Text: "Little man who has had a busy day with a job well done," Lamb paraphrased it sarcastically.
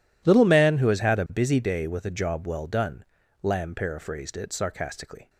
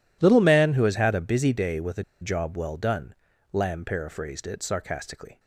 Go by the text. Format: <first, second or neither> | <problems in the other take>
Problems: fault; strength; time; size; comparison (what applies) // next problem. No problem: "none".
first | pauses between "a" and "job"; slight; at 2.0 s; 0.18 s long